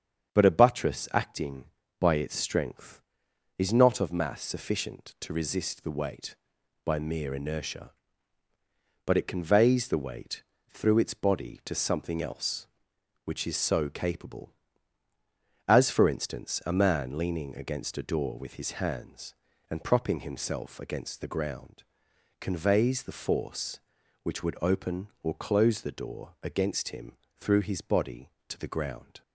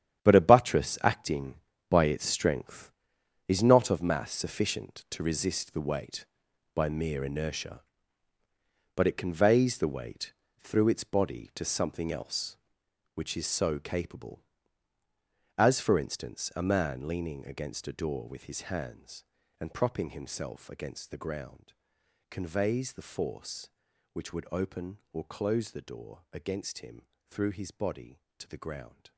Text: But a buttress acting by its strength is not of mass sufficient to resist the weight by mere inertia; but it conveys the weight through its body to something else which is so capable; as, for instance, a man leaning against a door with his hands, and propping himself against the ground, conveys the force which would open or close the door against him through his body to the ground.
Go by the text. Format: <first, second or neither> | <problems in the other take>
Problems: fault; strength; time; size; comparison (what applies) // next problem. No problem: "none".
first | gets quieter; strong; throughout; 13 dB // starts louder than the rest; strong; until 1.2 s; 10 dB; strong in the first // pauses between "weight" and "through"; slight; at 10.3 s; 0.24 s long; slight in the first // pauses between "him" and "through"; slight; at 27.0 s; 0.20 s long; slight in the first